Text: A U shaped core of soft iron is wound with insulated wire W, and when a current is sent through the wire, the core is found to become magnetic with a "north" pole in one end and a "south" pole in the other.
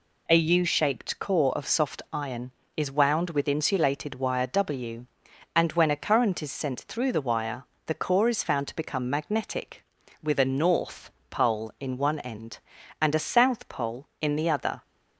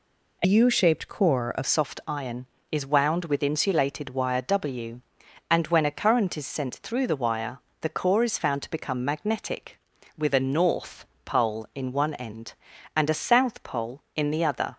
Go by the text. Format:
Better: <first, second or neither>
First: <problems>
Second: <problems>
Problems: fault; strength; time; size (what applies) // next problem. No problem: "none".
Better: first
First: pauses between "north" and "pole"; slight; at 11.0 s; 0.22 s long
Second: changes voice from "U" to "of"; from 0.4 to 1.6 s; 1.2 s long // pauses between "north" and "pole"; slight; at 11.0 s; 0.22 s long